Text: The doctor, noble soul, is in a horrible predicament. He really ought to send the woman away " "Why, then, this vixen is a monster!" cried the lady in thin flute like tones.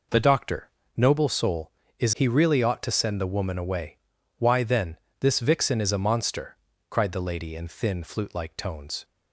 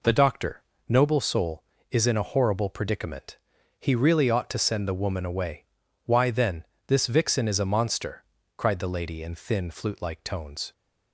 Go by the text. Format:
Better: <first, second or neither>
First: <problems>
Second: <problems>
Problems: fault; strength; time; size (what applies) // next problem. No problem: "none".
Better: second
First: skips "in a horrible predicament"; at 2.1 s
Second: none